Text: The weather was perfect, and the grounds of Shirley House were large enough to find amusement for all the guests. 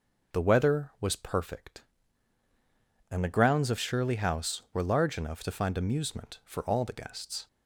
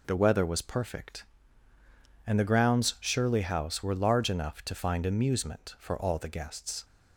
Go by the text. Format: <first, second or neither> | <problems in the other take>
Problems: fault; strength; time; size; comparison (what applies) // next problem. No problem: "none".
first | skips "of"; at 2.9 s